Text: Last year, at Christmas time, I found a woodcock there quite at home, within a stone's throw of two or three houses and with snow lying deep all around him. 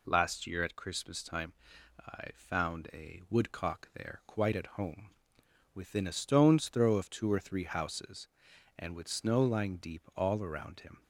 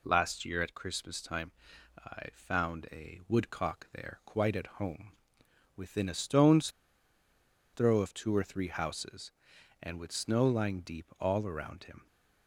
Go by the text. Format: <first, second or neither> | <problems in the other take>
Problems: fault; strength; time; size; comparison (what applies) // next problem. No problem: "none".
first | pauses between "stone's" and "throw"; at 6.7 s; 1.0 s long